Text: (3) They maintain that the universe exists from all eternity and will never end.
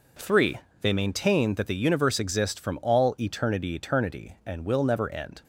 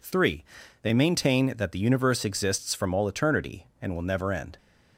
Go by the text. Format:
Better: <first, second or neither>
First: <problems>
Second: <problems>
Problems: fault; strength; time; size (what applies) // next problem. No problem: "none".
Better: second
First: says "eternity" twice; at 3.7 s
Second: none